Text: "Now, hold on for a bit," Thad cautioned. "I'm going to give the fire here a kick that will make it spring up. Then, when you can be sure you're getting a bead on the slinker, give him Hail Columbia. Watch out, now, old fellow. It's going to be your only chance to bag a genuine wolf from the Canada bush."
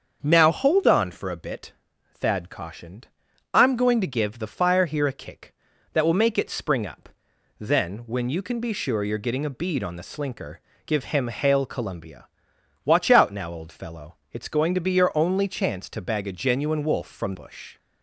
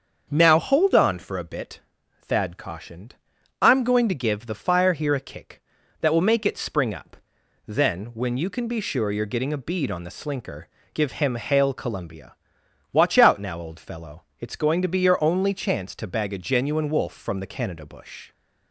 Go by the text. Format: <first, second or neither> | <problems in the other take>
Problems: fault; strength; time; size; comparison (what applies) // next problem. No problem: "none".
second | starts louder than the rest; until 1.2 s; 7 dB; also in the second // skips "the Canada"; at 17.3 s